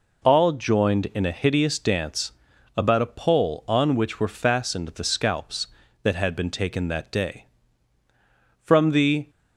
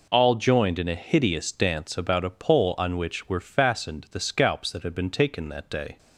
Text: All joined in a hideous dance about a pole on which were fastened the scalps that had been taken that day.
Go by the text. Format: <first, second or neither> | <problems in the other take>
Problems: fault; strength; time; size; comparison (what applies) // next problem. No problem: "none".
second | pauses between "dance" and "about"; at 2.3 s; 0.44 s long // goes on to say "From the"; noticeable; from 8.6 s on; 0.68 s long